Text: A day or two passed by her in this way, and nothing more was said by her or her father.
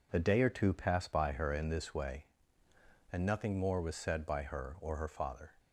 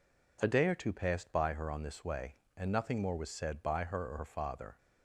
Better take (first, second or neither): first